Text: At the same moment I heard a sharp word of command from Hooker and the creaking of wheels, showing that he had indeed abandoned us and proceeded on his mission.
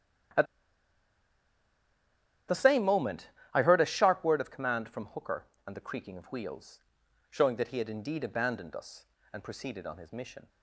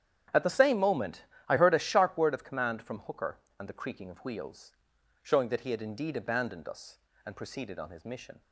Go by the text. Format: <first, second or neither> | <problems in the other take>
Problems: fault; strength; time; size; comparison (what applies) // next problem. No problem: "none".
second | starts louder than the rest; strong; until 3.6 s; 9.5 dB; strong in the second // pauses between "At" and "the"; strong; at 0.4 s; 2.0 s long // pauses between "moment" and "I"; slight; at 3.2 s; 0.24 s long; slight in the second